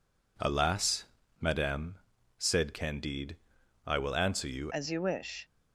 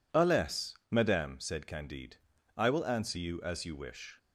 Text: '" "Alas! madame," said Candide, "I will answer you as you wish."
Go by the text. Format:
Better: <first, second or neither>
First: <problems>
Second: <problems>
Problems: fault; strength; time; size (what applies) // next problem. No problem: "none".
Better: second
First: changes voice at "as"; from 4.7 s on; 0.7 s long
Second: none